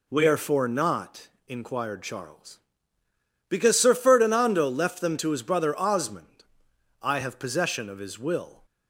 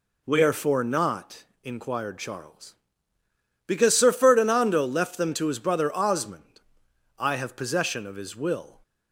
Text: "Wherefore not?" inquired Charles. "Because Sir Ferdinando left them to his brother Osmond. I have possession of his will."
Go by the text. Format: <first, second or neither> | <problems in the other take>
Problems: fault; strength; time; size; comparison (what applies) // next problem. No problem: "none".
neither | none